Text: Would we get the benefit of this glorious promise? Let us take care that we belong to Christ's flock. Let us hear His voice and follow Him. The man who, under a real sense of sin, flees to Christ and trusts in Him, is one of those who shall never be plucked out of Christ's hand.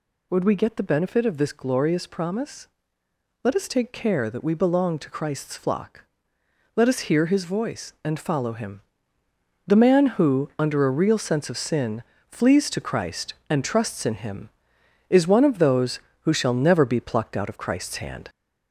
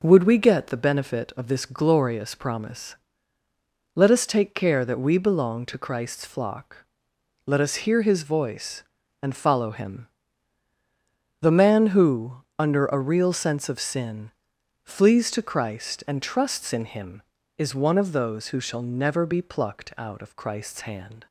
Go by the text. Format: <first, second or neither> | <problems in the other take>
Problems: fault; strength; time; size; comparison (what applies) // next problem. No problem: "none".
second | gets louder; slight; throughout; 2.5 dB